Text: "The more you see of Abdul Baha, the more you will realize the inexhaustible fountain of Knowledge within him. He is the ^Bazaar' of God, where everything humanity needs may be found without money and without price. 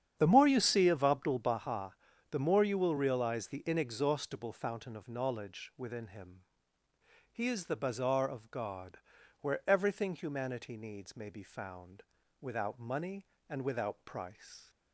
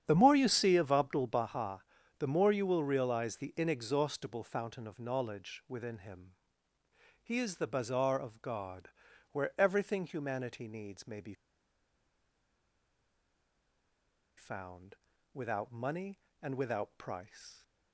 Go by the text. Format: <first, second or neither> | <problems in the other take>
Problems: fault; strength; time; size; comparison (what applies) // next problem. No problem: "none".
first | starts louder than the rest; strong; until 1.0 s; 9 dB; strong in the first // pauses between "be" and "found"; strong; at 11.3 s; 3.0 s long // pauses between "found" and "without"; slight; at 14.9 s; 0.36 s long; slight in the first